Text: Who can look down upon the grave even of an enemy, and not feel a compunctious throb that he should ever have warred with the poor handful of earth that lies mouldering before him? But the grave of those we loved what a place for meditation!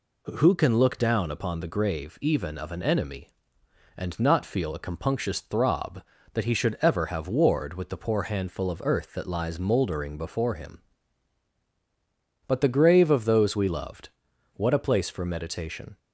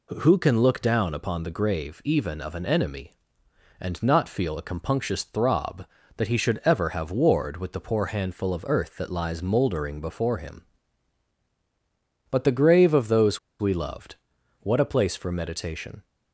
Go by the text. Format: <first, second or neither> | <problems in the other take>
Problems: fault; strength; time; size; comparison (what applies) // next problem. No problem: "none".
first | pauses between "those" and "we"; slight; at 13.3 s; 0.21 s long // pauses between "loved" and "what"; at 14.1 s; 0.44 s long; also in the first